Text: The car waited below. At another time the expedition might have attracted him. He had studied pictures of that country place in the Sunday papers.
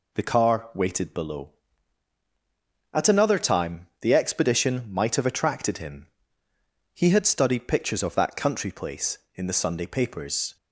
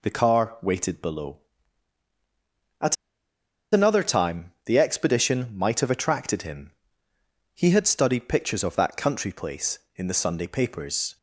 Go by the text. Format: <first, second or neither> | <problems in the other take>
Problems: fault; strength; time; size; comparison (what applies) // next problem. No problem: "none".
first | pauses between "At" and "another"; noticeable; at 2.9 s; 0.77 s long